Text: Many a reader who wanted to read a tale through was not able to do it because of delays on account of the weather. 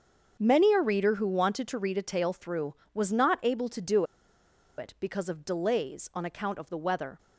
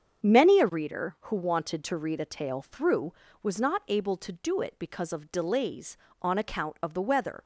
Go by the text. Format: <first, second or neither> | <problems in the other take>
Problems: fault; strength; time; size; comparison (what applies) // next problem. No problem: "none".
second | starts louder than the rest; until 1.4 s; 7 dB; strong in the second // pauses between "do" and "it"; noticeable; at 4.0 s; 0.74 s long